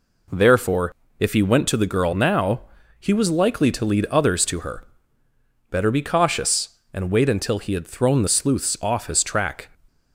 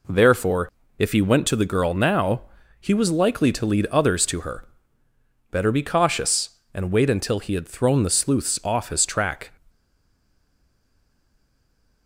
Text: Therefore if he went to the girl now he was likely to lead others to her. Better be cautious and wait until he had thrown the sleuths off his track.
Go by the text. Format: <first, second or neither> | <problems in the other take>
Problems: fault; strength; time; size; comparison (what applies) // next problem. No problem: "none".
first | pauses between "Therefore" and "if"; slight; at 0.7 s; 0.27 s long; slight in the first // pauses between "now" and "he"; at 2.4 s; 0.38 s long; also in the first // stays silent after the last word; from 9.6 s on; 2.4 s long